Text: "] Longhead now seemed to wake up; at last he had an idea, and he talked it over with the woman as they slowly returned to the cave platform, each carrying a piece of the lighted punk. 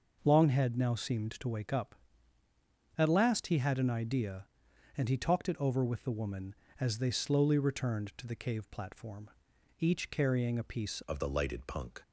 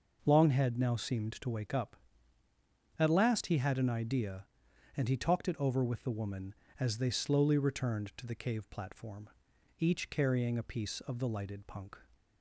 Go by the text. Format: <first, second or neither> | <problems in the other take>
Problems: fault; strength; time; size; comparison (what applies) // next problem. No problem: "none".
second | changes voice at "of"; from 11.0 s on; 1.0 s long